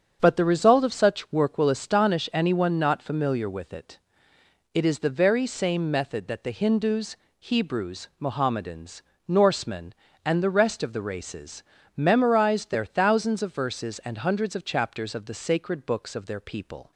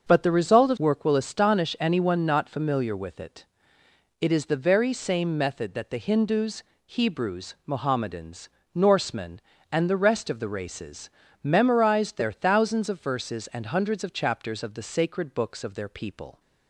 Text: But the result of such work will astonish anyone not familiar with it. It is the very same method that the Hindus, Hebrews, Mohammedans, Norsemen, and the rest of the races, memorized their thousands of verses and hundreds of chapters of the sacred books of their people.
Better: first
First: starts louder than the rest; strong; until 1.2 s; 7 dB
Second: starts louder than the rest; until 1.1 s; 6.5 dB // skips "such"; at 0.7 s

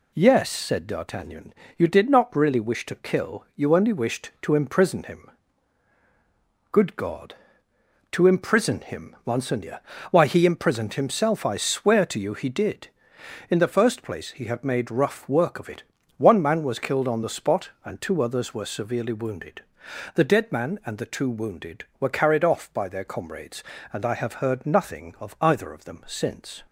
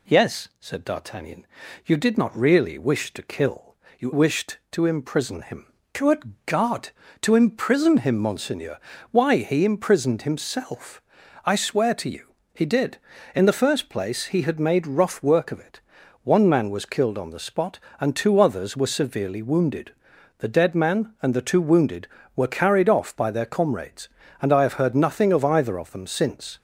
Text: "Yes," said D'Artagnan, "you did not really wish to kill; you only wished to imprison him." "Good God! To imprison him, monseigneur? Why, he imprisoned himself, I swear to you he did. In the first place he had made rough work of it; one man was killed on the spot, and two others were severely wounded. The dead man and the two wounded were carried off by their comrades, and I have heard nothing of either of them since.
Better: first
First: none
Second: skips "only"; at 4.1 s // pauses between "you" and "he"; slight; at 12.3 s; 0.20 s long

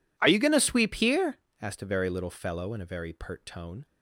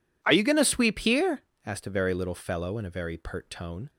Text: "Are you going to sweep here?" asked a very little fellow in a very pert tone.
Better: second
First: gets quieter; strong; throughout; 25.5 dB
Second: none

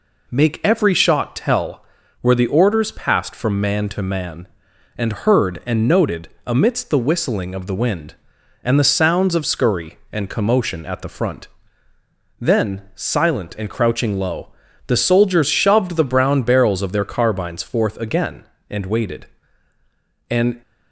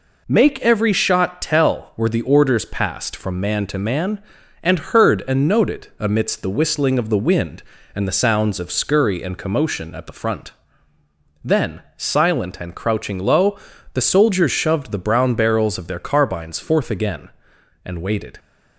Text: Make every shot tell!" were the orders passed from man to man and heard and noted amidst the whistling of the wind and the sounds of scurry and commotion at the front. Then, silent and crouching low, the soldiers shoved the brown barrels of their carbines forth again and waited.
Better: second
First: pauses between "noted" and "amidst"; slight; at 6.2 s; 0.18 s long // goes on to say "And"; slight; from 20.2 s on; 0.32 s long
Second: none

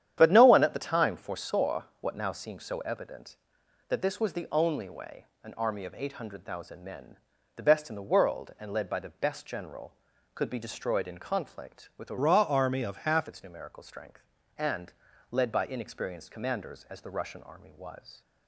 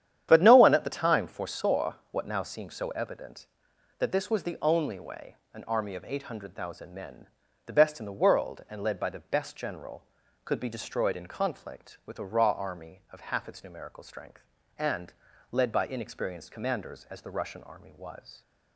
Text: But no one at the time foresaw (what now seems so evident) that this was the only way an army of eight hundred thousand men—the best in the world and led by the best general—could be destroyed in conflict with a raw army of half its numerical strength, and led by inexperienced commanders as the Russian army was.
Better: second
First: starts louder than the rest; strong; until 1.1 s; 10 dB // pauses between "way" and "an"; slight; at 5.2 s; 0.18 s long // changes voice from "raw" to "half"; from 12.1 to 13.2 s; 1.1 s long // pauses between "and" and "led"; slight; at 14.9 s; 0.36 s long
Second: starts louder than the rest; strong; until 1.3 s; 10 dB // pauses between "way" and "an"; slight; at 5.3 s; 0.18 s long // pauses between "and" and "led"; slight; at 15.1 s; 0.36 s long

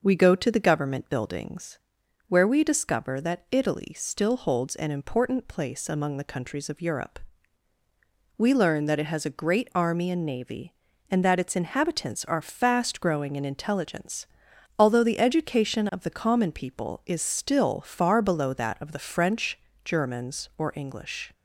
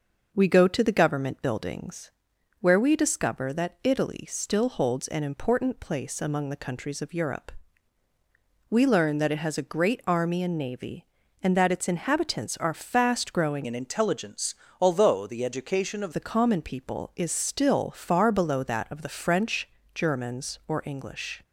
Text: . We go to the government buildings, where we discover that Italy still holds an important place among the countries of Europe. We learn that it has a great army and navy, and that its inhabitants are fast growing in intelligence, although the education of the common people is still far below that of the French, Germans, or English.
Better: first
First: none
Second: changes voice from "in" to "of"; from 13.6 to 16.1 s; 2.5 s long

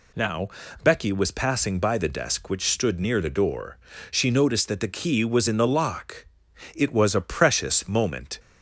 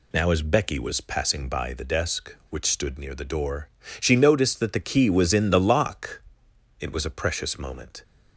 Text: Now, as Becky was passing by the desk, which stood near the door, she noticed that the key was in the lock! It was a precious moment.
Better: second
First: skips "as"; at 0.6 s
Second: none

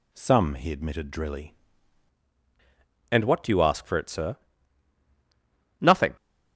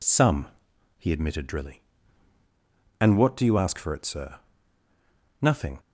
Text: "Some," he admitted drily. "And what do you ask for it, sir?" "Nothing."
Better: second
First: changes voice at "And"; from 3.1 s on; 3.0 s long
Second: none

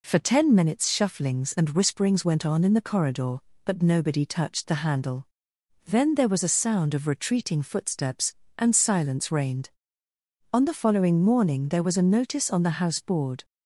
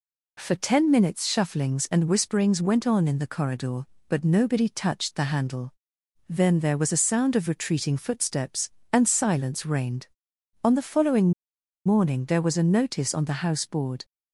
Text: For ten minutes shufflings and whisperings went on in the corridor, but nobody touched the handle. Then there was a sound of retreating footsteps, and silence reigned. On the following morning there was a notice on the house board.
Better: first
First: none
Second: pauses between "following" and "morning"; noticeable; at 11.3 s; 0.53 s long

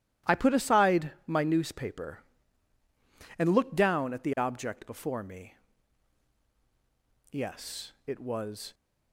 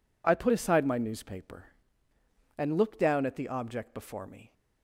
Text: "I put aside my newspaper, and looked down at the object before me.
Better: second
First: starts louder than the rest; strong; until 1.4 s; 13.5 dB // pauses between "aside" and "my"; slight; at 1.1 s; 0.16 s long // goes on to say "Yes it was"; from 7.3 s on; 1.4 s long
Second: none

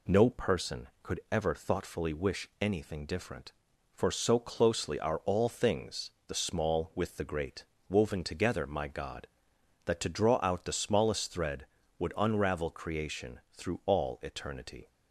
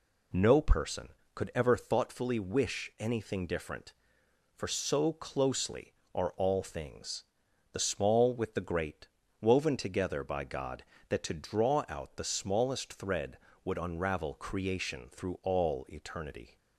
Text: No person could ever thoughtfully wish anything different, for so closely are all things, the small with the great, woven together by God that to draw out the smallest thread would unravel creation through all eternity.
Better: second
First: says "my" for "by"; at 8.6 s // pauses between "creation" and "through"; slight; at 13.3 s; 0.16 s long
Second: none

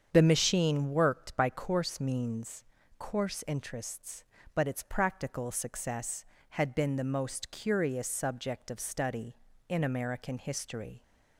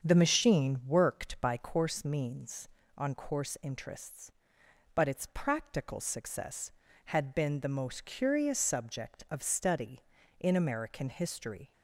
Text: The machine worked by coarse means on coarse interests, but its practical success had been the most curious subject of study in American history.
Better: second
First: starts louder than the rest; strong; until 1.1 s; 7.5 dB // skips "on"; at 2.8 s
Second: starts louder than the rest; strong; until 1.0 s; 7 dB

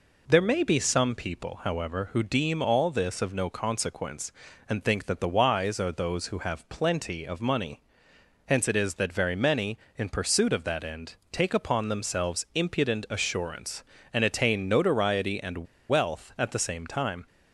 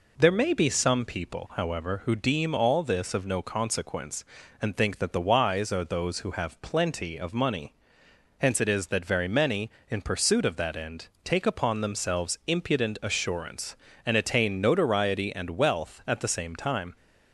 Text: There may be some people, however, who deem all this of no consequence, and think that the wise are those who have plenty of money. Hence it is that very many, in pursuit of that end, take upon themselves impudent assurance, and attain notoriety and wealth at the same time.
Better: second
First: pauses between "and" and "wealth"; slight; at 15.6 s; 0.26 s long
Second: none

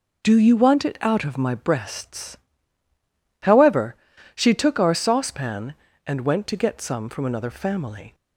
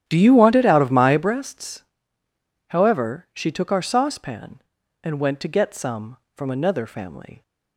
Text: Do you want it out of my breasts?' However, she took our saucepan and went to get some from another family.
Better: first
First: none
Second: starts louder than the rest; strong; until 1.4 s; 11.5 dB

